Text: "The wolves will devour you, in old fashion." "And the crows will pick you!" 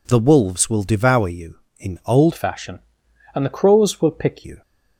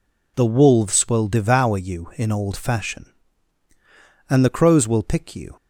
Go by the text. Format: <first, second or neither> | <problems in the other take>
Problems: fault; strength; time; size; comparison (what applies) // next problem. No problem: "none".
second | changes voice from "fashion" to "pick"; from 2.3 to 4.4 s; 2.1 s long